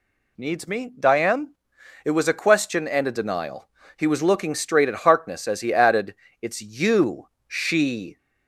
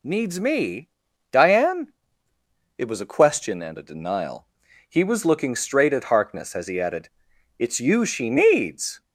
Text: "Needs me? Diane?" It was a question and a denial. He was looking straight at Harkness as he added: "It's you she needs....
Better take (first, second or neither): second